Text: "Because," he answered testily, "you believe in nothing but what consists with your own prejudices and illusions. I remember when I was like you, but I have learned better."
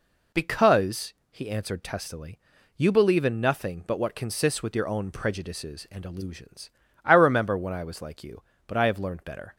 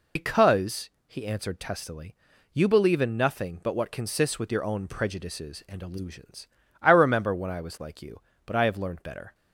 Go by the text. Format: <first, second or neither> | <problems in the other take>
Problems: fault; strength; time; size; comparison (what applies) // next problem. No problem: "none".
first | loses the start of "Because"; at 0.1 s; 45 ms